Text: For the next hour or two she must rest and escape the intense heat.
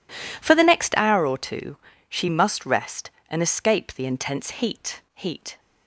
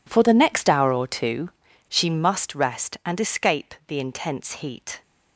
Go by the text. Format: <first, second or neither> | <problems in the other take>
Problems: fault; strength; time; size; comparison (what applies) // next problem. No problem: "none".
second | pauses between "two" and "she"; slight; at 1.7 s; 0.32 s long; also in the second // says "heat" twice; at 5.1 s